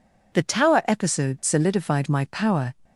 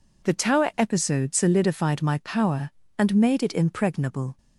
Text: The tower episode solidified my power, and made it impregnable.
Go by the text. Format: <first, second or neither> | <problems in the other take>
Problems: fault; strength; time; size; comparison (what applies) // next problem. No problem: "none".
second | stops before "and made it impregnable"; at 2.8 s